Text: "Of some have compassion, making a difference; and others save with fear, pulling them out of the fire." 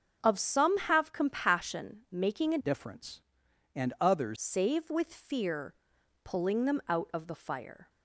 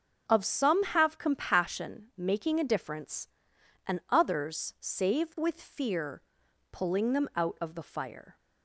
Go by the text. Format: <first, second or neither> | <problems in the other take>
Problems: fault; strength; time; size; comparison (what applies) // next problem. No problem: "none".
second | starts louder than the rest; until 1.2 s; 6.5 dB; also in the second // changes voice from "difference" to "others"; from 2.5 to 4.3 s; 1.8 s long